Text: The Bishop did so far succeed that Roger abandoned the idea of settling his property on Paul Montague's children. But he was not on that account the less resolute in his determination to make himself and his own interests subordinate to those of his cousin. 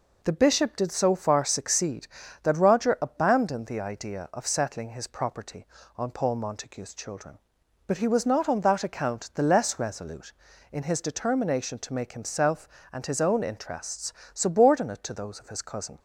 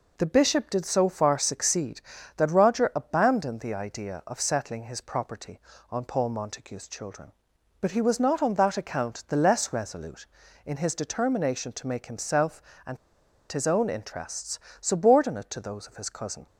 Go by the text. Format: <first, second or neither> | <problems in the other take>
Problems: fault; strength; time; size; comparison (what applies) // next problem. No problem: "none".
first | pauses between "and" and "his"; noticeable; at 12.9 s; 0.54 s long // pauses between "interests" and "subordinate"; slight; at 14.5 s; 0.22 s long; slight in the first